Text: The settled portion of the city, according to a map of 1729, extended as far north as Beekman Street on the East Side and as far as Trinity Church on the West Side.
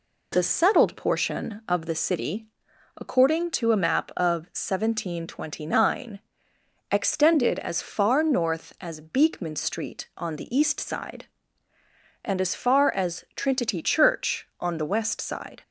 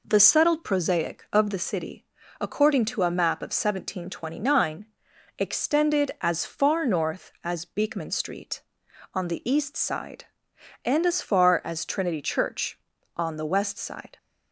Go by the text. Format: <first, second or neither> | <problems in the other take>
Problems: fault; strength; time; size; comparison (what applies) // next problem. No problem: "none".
first | says "prosaic" for "portion"; at 0.6 s